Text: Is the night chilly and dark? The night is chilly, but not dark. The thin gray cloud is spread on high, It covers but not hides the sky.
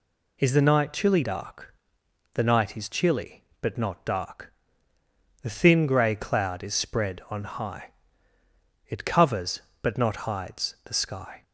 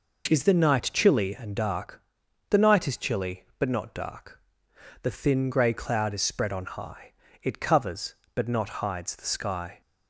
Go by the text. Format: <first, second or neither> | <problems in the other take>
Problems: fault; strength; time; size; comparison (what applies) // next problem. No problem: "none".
second | skips "and"; at 1.2 s